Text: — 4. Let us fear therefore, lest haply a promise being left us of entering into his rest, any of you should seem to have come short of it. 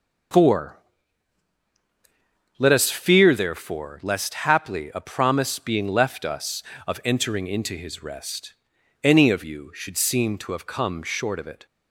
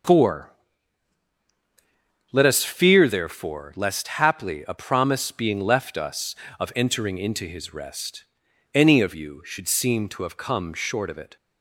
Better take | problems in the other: neither | none

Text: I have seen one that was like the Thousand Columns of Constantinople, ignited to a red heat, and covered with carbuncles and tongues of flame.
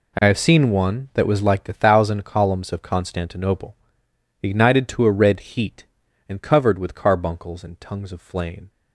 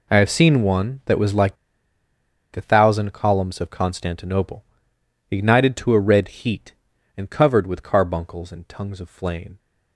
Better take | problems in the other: first | pauses between "like" and "the"; noticeable; at 1.5 s; 0.96 s long

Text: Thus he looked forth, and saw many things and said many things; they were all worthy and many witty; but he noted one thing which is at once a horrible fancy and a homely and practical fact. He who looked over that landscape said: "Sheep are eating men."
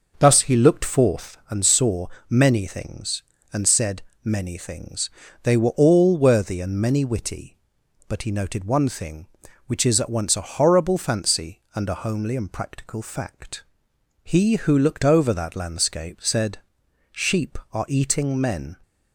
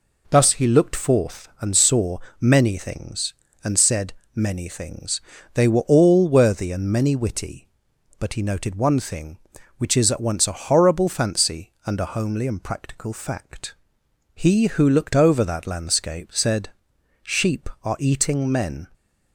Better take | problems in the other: second | starts louder than the rest; noticeable; until 1.4 s; 6 dB // pauses between "saw" and "many"; slight; at 2.0 s; 0.22 s long; slight in the second // pauses between "said" and "many"; slight; at 4.0 s; 0.22 s long; slight in the second

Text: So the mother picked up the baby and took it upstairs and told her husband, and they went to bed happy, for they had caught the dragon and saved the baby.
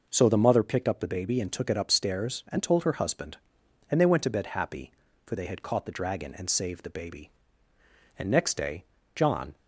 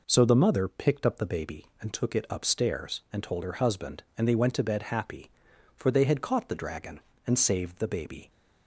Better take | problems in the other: second | goes on to say "And next day John"; from 8.1 s on; 1.3 s long

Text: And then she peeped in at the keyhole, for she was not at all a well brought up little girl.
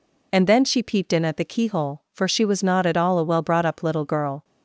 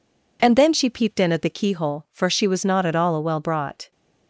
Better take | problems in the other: first | stops before "up little girl"; at 3.9 s

